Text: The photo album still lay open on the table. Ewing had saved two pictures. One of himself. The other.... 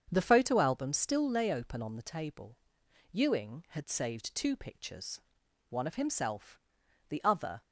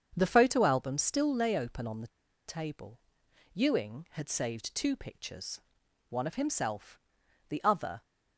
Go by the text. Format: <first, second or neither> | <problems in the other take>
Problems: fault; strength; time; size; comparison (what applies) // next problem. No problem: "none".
first | starts louder than the rest; strong; until 1.1 s; 7 dB; strong in the first // pauses between "the" and "table"; at 2.0 s; 0.39 s long